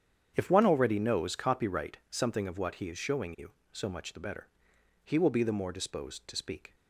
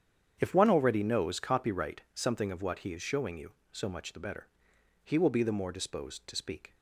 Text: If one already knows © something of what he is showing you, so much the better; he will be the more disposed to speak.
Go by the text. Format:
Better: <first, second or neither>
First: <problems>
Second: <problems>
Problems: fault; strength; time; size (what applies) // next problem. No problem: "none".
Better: neither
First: starts louder than the rest; strong; until 1.3 s; 8.5 dB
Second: starts louder than the rest; strong; until 1.4 s; 8.5 dB